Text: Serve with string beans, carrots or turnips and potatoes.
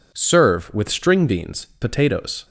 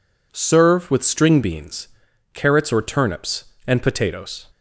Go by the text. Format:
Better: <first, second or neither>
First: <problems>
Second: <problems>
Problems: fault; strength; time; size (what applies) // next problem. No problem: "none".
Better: second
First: skips "carrots or turnips and"; at 1.7 s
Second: none